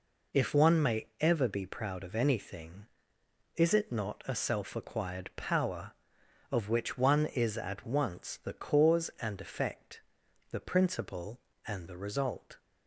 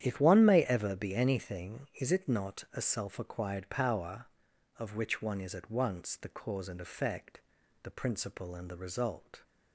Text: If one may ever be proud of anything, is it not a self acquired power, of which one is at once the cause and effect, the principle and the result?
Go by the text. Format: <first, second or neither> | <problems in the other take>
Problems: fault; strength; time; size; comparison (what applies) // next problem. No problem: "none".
first | starts louder than the rest; strong; until 1.0 s; 10 dB // skips "proud of"; at 1.1 s